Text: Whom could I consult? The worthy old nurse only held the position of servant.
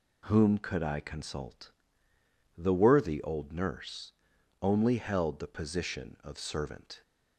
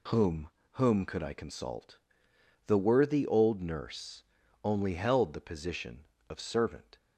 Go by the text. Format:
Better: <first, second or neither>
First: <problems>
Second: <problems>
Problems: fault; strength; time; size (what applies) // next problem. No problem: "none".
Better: first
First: pauses between "nurse" and "only"; noticeable; at 4.1 s; 0.50 s long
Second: says "Whom" twice; at 0.7 s // pauses between "nurse" and "only"; at 4.2 s; 0.40 s long